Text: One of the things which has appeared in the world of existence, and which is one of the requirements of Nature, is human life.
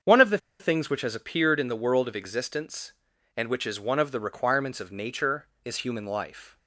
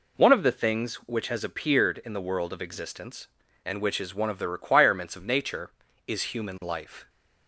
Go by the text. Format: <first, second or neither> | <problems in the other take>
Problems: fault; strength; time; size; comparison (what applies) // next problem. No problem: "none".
second | starts louder than the rest; strong; until 1.2 s; 7 dB // pauses between "the" and "things"; slight; at 0.3 s; 0.22 s long